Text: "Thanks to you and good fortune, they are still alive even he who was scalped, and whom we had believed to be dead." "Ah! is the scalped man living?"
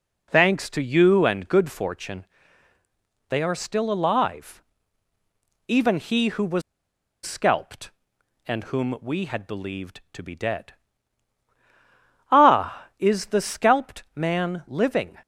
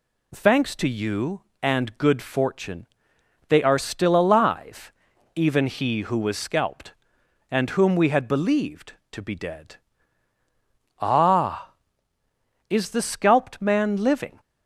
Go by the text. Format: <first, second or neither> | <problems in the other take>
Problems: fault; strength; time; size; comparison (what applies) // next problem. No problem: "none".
second | pauses between "alive" and "even"; at 4.6 s; 1.0 s long; also in the second // pauses between "was" and "scalped"; noticeable; at 6.6 s; 0.63 s long